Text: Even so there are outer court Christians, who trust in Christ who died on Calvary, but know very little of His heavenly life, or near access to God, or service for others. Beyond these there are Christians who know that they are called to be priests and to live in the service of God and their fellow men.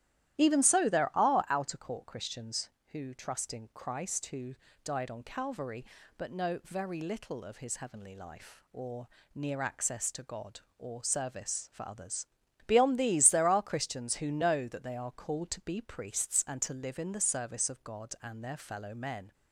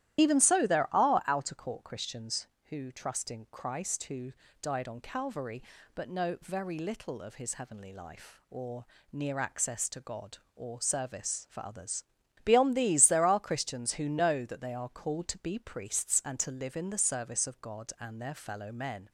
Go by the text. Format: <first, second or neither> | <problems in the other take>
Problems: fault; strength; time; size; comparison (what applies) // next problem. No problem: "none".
first | loses the start of "Even"; at 0.1 s; 40 ms // starts louder than the rest; strong; until 1.2 s; 12.5 dB; strong in the first // pauses between "who" and "died"; slight; at 4.3 s; 0.32 s long; slight in the first // pauses between "or" and "near"; slight; at 8.8 s; 0.28 s long; slight in the first